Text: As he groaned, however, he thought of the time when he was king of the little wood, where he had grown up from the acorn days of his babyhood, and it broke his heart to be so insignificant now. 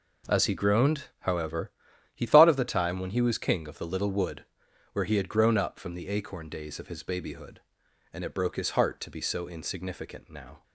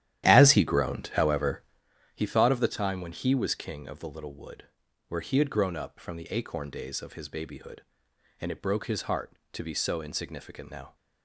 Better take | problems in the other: first | starts louder than the rest; strong; until 1.9 s; 12 dB

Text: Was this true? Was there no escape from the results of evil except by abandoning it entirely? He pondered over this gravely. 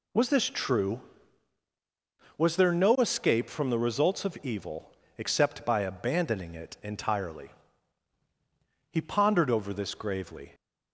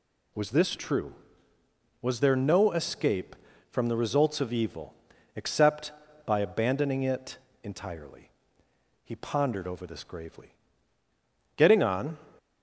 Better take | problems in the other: first | pauses between "evil" and "except"; at 4.9 s; 0.42 s long; slight in the first // pauses between "it" and "entirely"; slight; at 7.3 s; 0.26 s long // goes on to say "Getting on"; noticeable; from 11.5 s on; 0.62 s long

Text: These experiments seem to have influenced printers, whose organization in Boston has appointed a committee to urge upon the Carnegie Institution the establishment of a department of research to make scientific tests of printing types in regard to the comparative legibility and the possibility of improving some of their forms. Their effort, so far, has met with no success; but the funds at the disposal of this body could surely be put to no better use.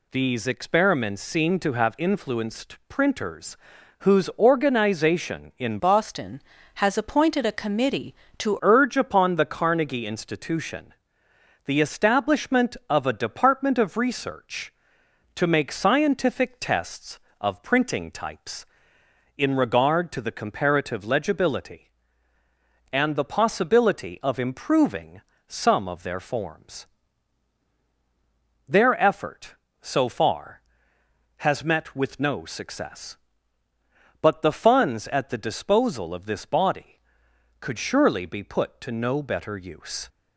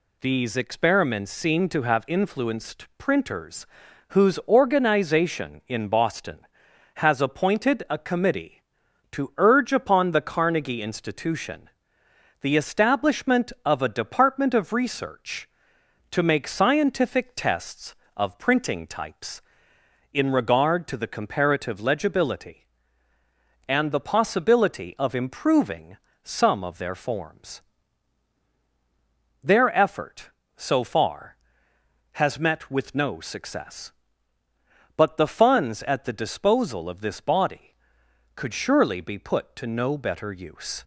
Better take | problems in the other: second | changes voice from "Boston" to "to"; from 5.7 to 8.5 s; 2.8 s long // pauses between "Institution" and "the"; noticeable; at 10.9 s; 0.74 s long; noticeable in the second // pauses between "improving" and "some"; slight; at 25.2 s; 0.26 s long; slight in the second

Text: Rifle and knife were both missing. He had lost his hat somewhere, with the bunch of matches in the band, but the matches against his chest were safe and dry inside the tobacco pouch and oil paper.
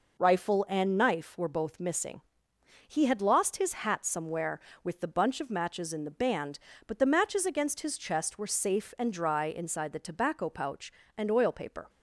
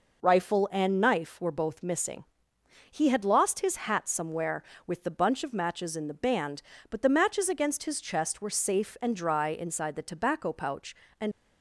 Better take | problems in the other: first | stops before "oil paper"; at 11.3 s

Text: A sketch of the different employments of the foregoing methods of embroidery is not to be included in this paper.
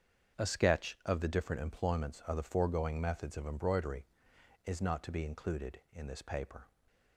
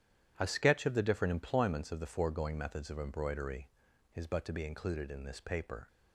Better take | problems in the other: first | starts louder than the rest; strong; until 1.3 s; 10.5 dB; strong in the first // says "but" for "not"; at 4.2 s

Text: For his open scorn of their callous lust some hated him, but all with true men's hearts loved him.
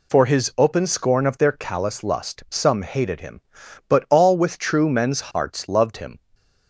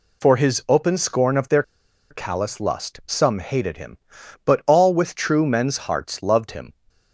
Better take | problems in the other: first | pauses between "their" and "callous"; noticeable; at 1.6 s; 0.47 s long

